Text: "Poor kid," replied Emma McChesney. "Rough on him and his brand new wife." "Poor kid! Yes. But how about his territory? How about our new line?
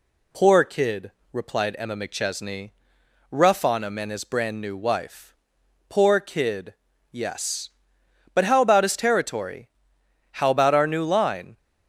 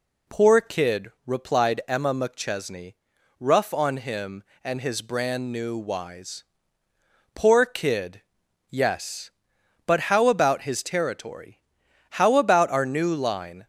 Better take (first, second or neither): first